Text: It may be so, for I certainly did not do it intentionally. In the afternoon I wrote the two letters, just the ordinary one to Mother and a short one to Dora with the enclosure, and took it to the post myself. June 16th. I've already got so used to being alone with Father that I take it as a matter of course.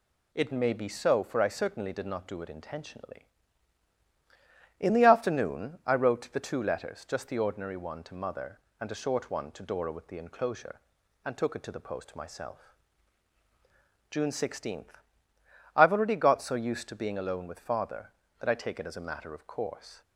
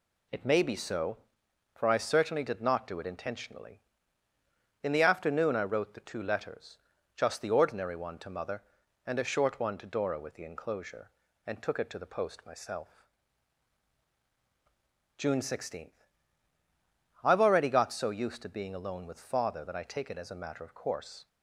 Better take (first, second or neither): neither